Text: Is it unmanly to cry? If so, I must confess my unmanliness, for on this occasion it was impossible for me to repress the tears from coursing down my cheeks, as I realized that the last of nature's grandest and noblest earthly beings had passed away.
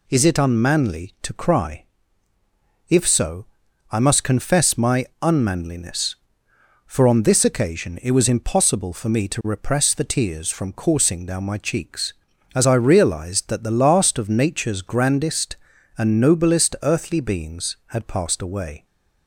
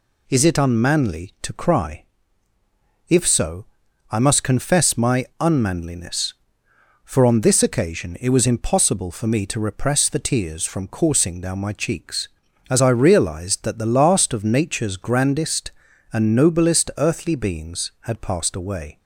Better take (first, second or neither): neither